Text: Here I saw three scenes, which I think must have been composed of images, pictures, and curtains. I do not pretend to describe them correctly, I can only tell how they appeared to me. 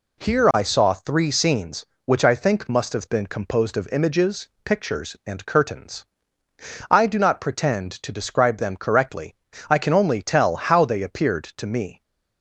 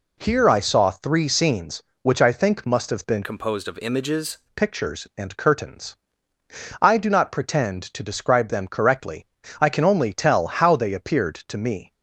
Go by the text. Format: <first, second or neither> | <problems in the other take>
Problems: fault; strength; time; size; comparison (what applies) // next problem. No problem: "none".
first | changes voice from "composed" to "images"; from 3.2 to 4.3 s; 1.1 s long